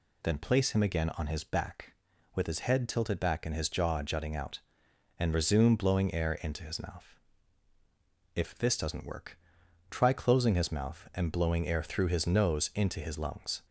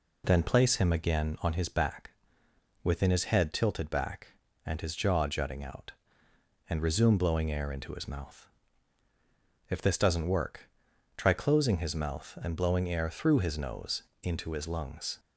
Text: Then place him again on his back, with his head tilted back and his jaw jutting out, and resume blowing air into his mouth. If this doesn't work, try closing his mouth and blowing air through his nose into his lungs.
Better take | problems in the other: first | says "within" for "with"; at 2.8 s // pauses between "nose" and "into"; slight; at 14.0 s; 0.22 s long

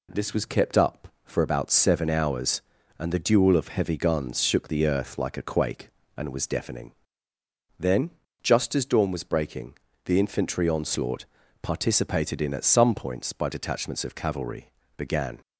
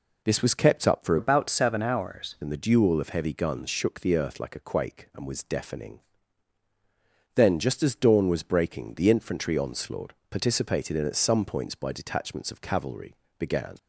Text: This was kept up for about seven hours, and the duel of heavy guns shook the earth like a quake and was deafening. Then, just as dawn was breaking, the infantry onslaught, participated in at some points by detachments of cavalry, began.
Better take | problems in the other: first | changes voice from "about" to "hours"; from 1.1 to 2.3 s; 1.2 s long

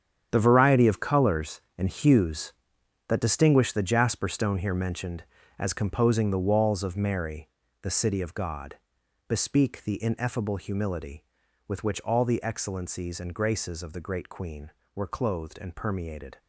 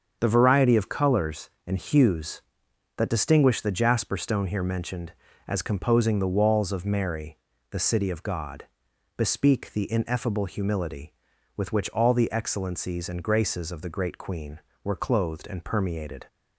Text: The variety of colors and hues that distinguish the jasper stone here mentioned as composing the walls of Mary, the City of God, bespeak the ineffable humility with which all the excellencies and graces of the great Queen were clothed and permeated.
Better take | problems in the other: second | gets quieter; strong; throughout; 12 dB // starts louder than the rest; strong; until 1.3 s; 9 dB; strong in the second

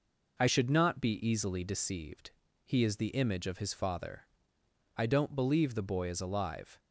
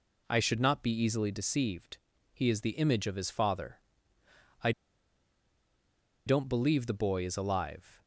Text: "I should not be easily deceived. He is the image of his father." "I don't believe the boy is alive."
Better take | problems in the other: first | pauses between "I" and "don't"; strong; at 4.7 s; 1.5 s long

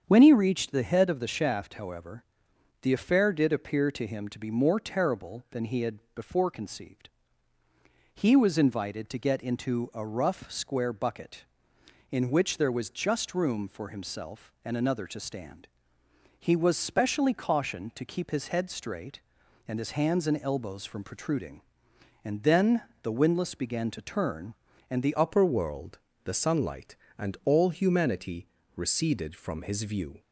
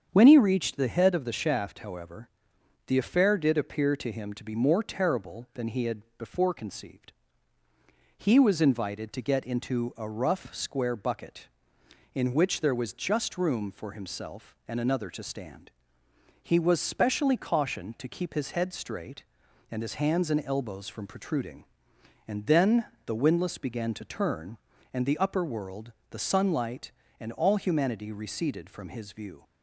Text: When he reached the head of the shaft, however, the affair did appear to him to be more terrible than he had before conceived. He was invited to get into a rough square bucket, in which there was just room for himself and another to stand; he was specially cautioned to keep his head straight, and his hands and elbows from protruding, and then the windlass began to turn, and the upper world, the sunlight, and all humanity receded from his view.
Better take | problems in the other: second | starts louder than the rest; strong; until 1.0 s; 7.5 dB; strong in the second // pauses between "had" and "before"; slight; at 5.9 s; 0.16 s long; slight in the second // pauses between "then" and "the"; slight; at 22.8 s; 0.22 s long; slight in the second // changes voice at "upper"; from 25.1 s on; 5.0 s long // pauses between "humanity" and "receded"; slight; at 28.4 s; 0.30 s long

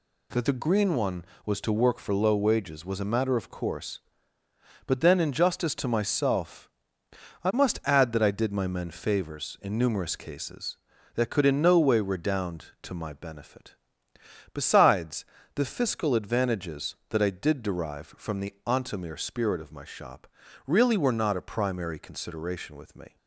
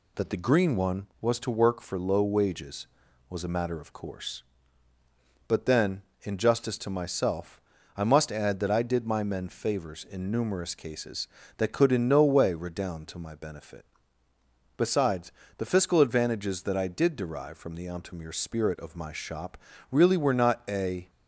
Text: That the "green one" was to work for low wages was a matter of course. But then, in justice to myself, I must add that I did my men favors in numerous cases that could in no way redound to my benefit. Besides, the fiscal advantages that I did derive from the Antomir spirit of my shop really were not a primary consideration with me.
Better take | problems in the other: first | pauses between "shop" and "really"; slight; at 19.5 s; 0.34 s long; also in the first // stops before "primary consideration with me"; at 21.0 s

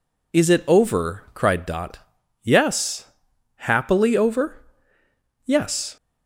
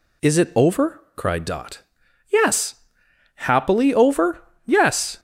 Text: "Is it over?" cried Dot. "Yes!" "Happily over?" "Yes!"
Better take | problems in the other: neither | none

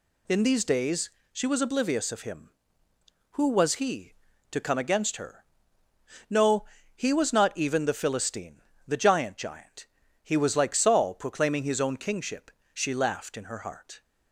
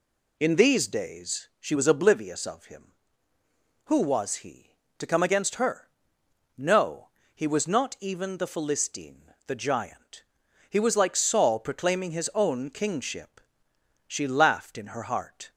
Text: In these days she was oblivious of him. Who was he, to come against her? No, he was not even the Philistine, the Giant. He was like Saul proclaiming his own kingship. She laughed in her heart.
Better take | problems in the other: second | pauses between "days" and "she"; slight; at 1.1 s; 0.20 s long // says "Giant" twice; at 9.3 s

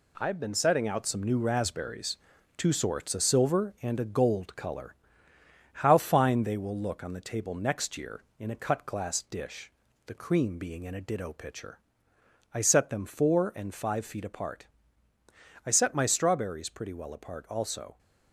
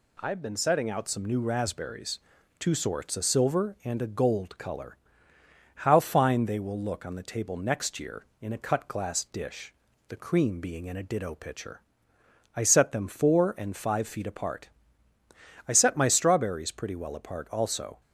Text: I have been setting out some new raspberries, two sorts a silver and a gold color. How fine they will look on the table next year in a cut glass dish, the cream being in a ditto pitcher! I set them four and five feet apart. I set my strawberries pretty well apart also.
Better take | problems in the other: second | gets quieter; throughout; 6.5 dB

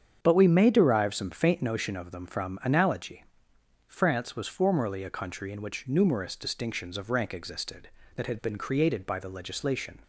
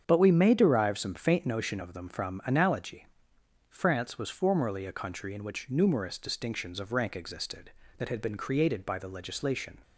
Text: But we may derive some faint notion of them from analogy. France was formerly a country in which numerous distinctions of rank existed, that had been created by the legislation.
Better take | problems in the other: neither | starts louder than the rest; strong; the same in both

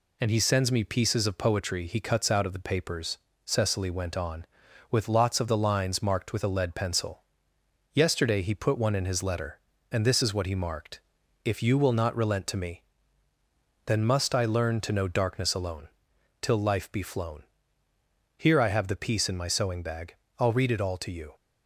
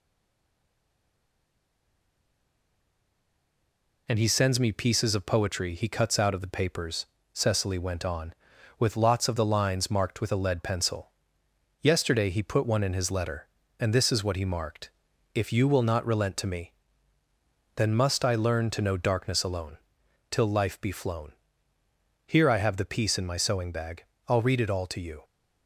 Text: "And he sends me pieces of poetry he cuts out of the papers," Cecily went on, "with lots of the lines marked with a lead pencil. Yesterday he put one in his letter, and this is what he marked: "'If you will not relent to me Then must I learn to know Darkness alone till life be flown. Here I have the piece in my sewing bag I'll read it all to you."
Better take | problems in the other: first | stays silent before the first word; strong; until 4.0 s; 4.0 s long // pauses between "me" and "Then"; at 16.7 s; 1.0 s long; also in the first // pauses between "alone" and "till"; noticeable; at 19.7 s; 0.52 s long; noticeable in the first // pauses between "bag" and "I'll"; slight; at 24.0 s; 0.24 s long; slight in the first

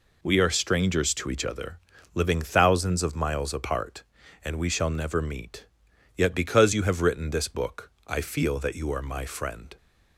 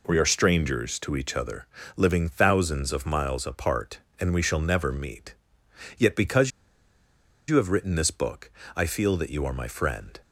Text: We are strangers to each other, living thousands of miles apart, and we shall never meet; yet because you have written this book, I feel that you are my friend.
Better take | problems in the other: first | pauses between "because" and "you"; at 6.5 s; 0.98 s long

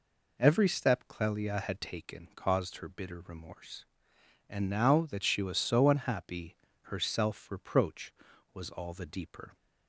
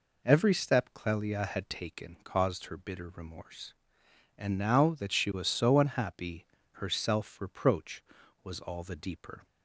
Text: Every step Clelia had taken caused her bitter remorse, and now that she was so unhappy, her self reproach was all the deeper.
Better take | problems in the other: neither | none

